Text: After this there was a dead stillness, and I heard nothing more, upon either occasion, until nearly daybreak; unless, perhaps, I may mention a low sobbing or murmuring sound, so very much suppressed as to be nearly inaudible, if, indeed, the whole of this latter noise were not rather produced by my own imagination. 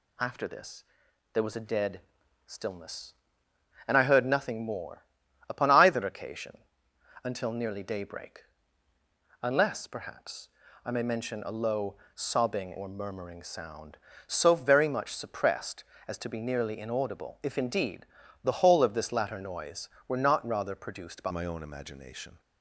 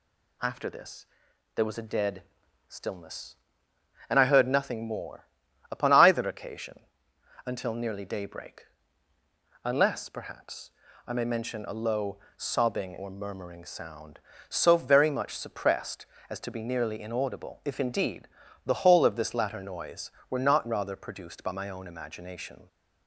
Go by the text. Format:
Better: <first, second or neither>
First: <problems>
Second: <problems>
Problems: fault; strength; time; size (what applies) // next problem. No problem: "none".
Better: second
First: pauses between "this" and "there"; noticeable; at 0.8 s; 0.50 s long // pauses between "dead" and "stillness"; noticeable; at 2.0 s; 0.46 s long // pauses between "low" and "sobbing"; slight; at 11.9 s; 0.18 s long // changes voice at "my"; from 21.3 s on; 1.0 s long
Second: pauses between "this" and "there"; noticeable; at 1.0 s; 0.50 s long // pauses between "dead" and "stillness"; noticeable; at 2.2 s; 0.46 s long // pauses between "low" and "sobbing"; slight; at 12.1 s; 0.18 s long